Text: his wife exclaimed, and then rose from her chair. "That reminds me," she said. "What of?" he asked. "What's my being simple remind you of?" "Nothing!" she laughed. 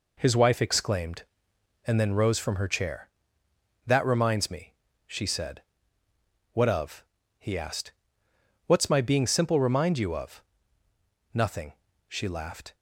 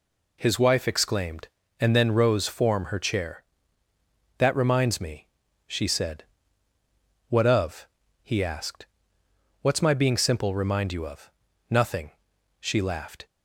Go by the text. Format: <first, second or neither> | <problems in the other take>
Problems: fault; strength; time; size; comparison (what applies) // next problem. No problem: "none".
first | says "form" for "from"; at 2.4 s